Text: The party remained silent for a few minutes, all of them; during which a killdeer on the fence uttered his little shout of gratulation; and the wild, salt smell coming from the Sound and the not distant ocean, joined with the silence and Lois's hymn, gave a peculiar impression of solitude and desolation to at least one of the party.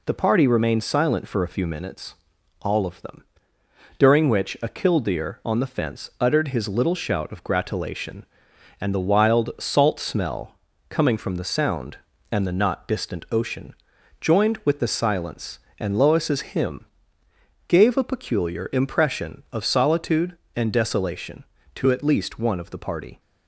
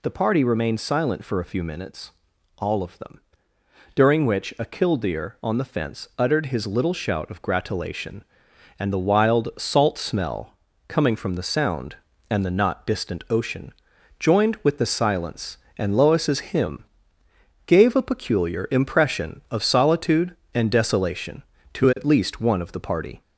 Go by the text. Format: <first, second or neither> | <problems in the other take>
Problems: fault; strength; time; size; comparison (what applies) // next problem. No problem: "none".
first | gets louder; slight; throughout; 2 dB // pauses between "smell" and "coming"; slight; at 10.5 s; 0.32 s long; slight in the first